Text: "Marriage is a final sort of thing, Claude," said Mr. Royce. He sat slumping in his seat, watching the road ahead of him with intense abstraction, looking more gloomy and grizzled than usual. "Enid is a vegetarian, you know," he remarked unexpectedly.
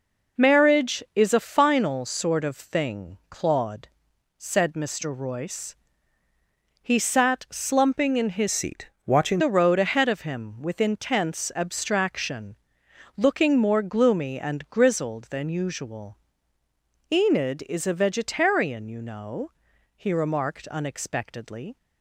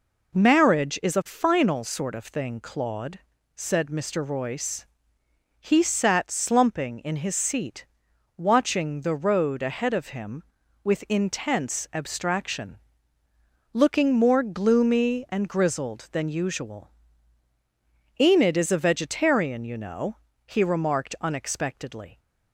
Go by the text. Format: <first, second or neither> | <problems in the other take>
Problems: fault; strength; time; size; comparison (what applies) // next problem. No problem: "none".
second | changes voice from "seat" to "watching"; from 8.5 to 9.3 s; 0.8 s long